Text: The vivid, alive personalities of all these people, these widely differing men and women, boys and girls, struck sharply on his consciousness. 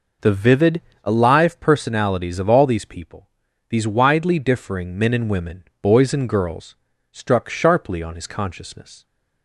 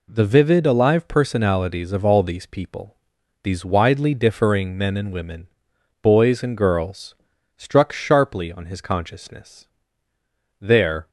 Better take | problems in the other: first | goes on to say "There"; from 10.5 s on; 0.50 s long

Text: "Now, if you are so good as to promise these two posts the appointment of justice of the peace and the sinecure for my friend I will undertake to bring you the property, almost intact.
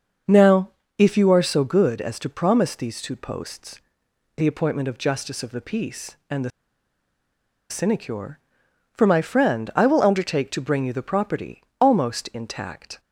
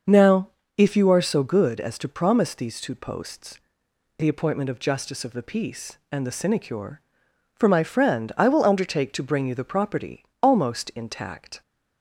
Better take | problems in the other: second | starts louder than the rest; until 1.5 s; 6.5 dB; also in the second // pauses between "posts" and "the"; noticeable; at 3.8 s; 0.56 s long; noticeable in the second // pauses between "the" and "sinecure"; at 6.5 s; 1.1 s long

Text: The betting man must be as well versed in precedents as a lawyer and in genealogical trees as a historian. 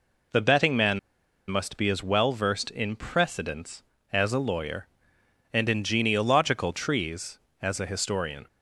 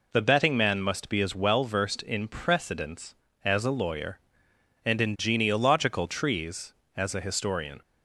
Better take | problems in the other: second | pauses between "man" and "must"; noticeable; at 0.9 s; 0.50 s long

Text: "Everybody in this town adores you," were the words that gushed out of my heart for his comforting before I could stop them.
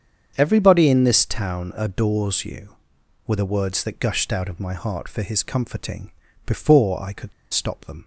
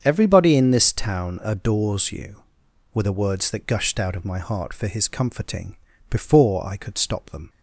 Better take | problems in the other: second | starts louder than the rest; strong; until 1.3 s; 7.5 dB; strong in the second // pauses between "comforting" and "before"; at 6.0 s; 0.38 s long; also in the second // pauses between "could" and "stop"; slight; at 7.3 s; 0.21 s long

